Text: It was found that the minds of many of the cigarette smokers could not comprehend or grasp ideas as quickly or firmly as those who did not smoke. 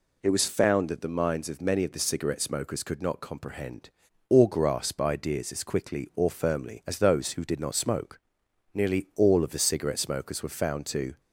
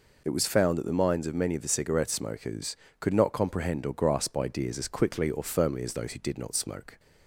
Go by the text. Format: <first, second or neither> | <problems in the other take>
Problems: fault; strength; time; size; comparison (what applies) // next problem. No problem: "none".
second | goes on to say "Nearly all of the cigarette smokers were found to"; strong; from 8.7 s on; 2.4 s long